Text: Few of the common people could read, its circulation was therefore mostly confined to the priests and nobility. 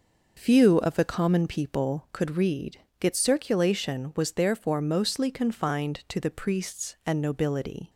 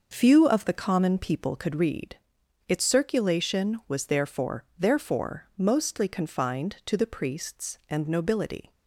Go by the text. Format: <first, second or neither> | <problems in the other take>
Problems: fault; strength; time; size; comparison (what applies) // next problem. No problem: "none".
first | starts louder than the rest; noticeable; until 1.1 s; 6 dB // says "therefore" twice; at 4.7 s